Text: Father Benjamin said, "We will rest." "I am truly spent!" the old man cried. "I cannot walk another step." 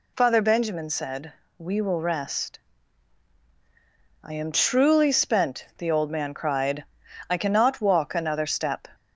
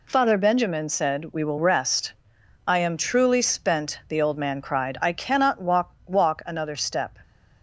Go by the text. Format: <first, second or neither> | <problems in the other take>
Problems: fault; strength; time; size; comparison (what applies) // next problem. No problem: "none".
first | says "walk" twice; at 6.0 s